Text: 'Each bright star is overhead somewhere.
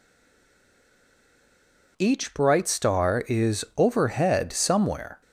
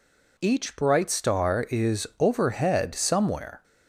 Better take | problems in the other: second | stays silent before the first word; noticeable; until 1.9 s; 1.9 s long

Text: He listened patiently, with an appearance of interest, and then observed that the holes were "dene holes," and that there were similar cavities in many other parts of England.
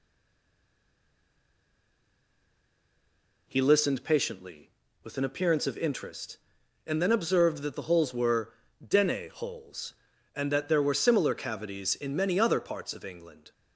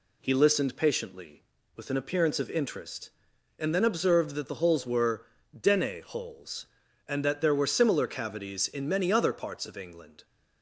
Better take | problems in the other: second | stays silent before the first word; strong; until 3.4 s; 3.4 s long // pauses between "were" and "dene"; slight; at 8.5 s; 0.34 s long; slight in the second

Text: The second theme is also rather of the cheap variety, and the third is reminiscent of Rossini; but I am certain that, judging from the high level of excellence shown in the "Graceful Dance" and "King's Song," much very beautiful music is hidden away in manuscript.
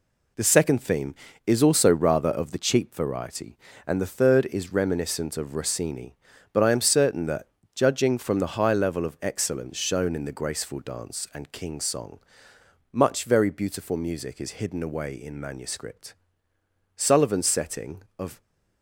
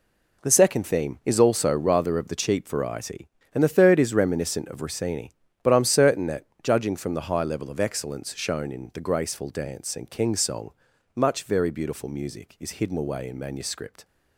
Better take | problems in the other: second | goes on to say "Sullivan's setting of"; from 16.9 s on; 1.4 s long

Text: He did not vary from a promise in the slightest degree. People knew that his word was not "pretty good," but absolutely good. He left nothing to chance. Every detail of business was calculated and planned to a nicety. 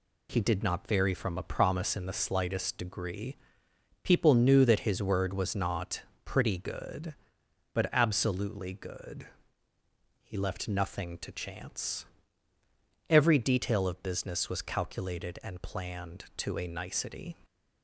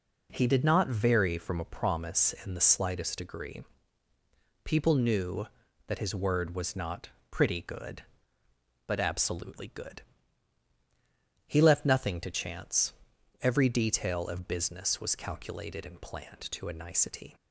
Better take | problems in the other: neither | pauses between "not" and "pretty"; slight; the same in both

